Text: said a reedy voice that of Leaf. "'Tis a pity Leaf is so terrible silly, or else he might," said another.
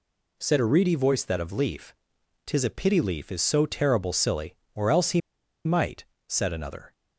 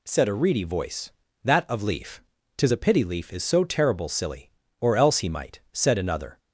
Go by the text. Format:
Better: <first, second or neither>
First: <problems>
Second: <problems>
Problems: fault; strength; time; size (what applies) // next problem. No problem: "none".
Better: second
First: pauses between "he" and "might"; noticeable; at 5.2 s; 0.46 s long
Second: none